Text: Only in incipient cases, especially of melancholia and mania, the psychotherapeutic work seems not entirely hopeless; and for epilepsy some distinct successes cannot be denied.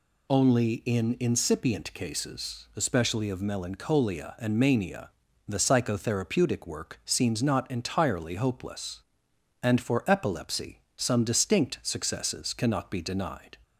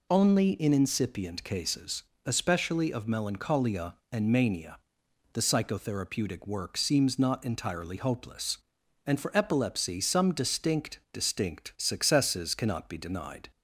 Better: first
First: none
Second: says "distinct" twice; at 11.1 s

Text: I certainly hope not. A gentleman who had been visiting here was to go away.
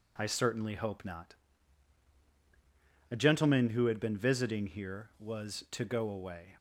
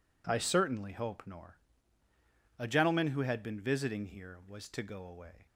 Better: first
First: none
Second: says "nor" for "not"; at 1.2 s

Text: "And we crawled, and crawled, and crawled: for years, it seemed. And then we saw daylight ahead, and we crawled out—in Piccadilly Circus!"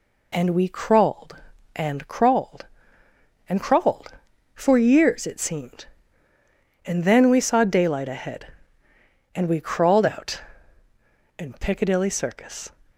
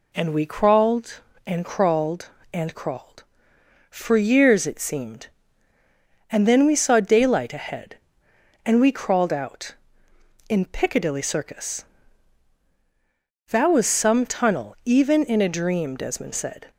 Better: first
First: none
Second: goes on to say "That was some tunnel even in a dream Desmond said"; strong; from 13.4 s on; 3.2 s long

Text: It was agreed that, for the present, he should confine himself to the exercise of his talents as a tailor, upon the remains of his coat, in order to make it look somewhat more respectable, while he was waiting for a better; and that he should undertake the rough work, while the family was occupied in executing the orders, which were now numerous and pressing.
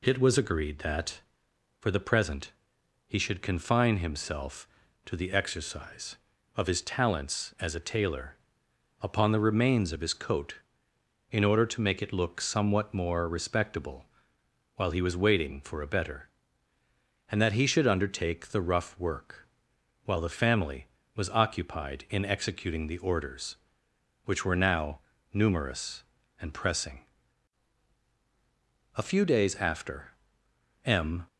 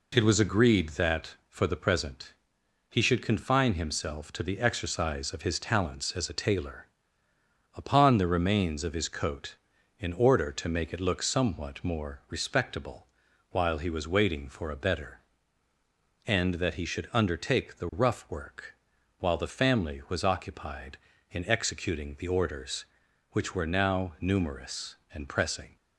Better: second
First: pauses between "now" and "numerous"; slight; at 24.9 s; 0.34 s long // goes on to say "A few days after M"; strong; from 28.9 s on; 2.3 s long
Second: none

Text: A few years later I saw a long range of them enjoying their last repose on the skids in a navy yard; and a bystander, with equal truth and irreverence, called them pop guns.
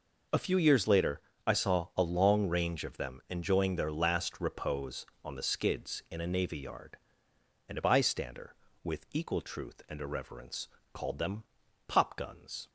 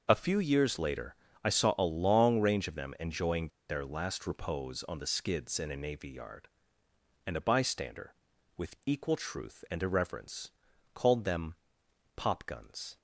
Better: first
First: pauses between "later" and "I"; slight; at 1.2 s; 0.26 s long // pauses between "them" and "pop"; at 11.4 s; 0.44 s long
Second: pauses between "later" and "I"; slight; at 1.1 s; 0.30 s long // pauses between "enjoying" and "their"; slight; at 3.4 s; 0.20 s long // pauses between "them" and "pop"; noticeable; at 11.5 s; 0.62 s long

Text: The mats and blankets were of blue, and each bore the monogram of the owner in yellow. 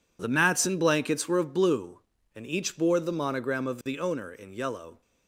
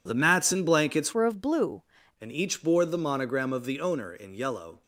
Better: first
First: none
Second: changes voice from "were" to "blue"; from 1.1 to 1.8 s; 0.7 s long

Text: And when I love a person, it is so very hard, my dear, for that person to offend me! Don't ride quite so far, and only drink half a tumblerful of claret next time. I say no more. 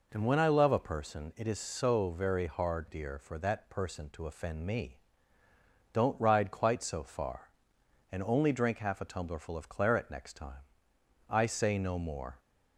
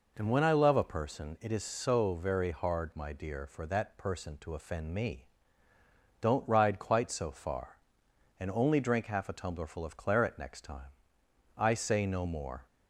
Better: second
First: skips "my"; at 2.8 s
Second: none

